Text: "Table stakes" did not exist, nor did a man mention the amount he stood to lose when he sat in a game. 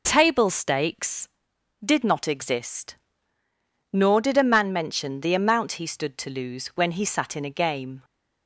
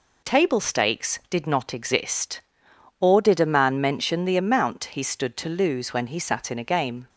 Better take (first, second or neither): first